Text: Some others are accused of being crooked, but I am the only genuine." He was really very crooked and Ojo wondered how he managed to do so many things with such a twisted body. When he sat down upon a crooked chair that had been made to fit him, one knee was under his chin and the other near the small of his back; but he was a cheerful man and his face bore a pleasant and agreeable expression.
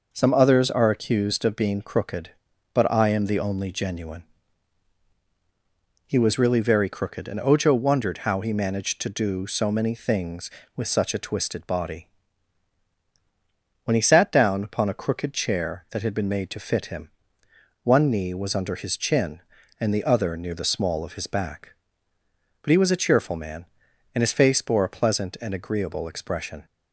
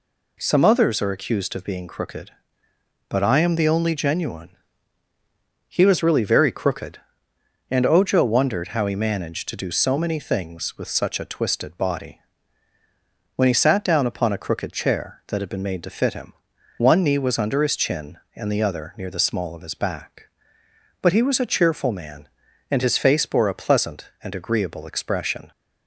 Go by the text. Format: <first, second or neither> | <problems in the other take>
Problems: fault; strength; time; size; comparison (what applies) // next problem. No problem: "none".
neither | none